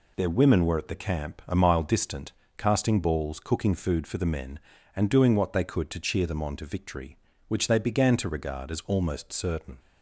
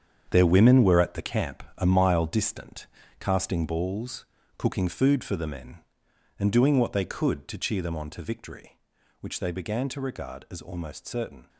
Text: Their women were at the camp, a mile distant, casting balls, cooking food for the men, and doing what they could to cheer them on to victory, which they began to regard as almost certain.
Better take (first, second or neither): first